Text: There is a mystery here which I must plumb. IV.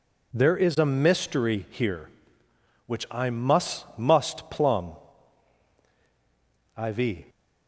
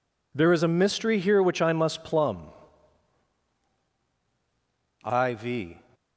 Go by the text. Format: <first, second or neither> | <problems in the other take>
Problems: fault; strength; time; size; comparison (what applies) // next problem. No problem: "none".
second | says "must" twice; at 3.9 s